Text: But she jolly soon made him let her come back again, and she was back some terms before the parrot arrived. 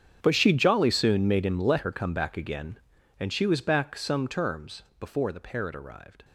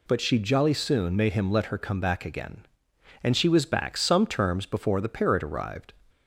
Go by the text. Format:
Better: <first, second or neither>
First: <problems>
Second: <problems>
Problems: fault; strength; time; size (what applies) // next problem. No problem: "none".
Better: second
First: gets quieter; strong; throughout; 19 dB // pauses between "terms" and "before"; slight; at 4.8 s; 0.16 s long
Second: none